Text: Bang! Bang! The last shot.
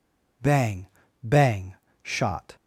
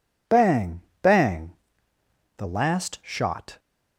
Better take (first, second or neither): second